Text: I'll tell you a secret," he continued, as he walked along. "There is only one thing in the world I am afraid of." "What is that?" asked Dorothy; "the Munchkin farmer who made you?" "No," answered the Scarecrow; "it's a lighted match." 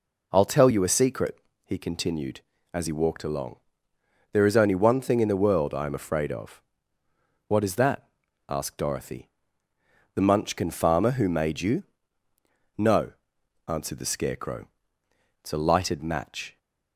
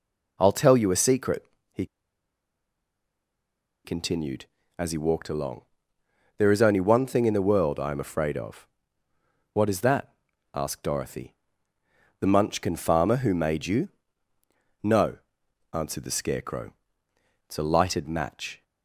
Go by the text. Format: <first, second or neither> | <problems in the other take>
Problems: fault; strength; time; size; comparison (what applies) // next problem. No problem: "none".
first | pauses between "he" and "continued"; strong; at 1.8 s; 1.9 s long